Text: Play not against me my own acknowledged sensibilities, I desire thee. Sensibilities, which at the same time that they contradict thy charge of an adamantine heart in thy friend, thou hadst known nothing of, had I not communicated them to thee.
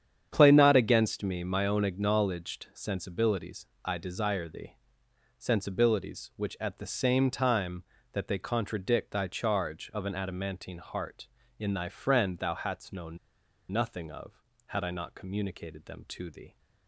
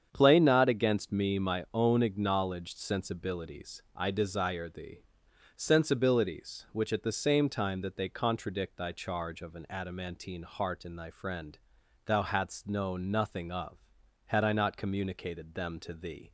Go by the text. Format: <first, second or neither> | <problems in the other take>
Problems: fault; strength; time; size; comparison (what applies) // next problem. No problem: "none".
second | starts louder than the rest; strong; until 1.3 s; 8.5 dB; strong in the second // pauses between "known" and "nothing"; noticeable; at 13.1 s; 0.54 s long